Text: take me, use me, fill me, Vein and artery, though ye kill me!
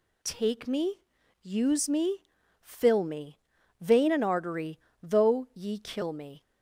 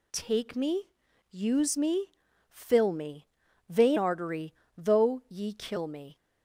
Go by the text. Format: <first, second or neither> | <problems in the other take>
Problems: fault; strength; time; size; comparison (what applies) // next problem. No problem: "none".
first | skips "and"; at 3.9 s